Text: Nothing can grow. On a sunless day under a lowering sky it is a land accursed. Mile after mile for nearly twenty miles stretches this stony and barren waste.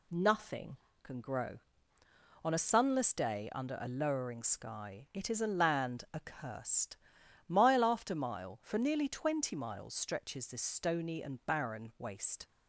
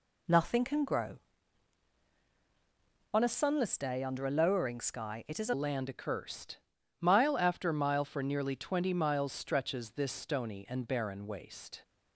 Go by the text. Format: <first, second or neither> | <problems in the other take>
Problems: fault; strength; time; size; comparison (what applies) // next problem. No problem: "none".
first | changes voice at "land"; from 5.5 s on; 6.3 s long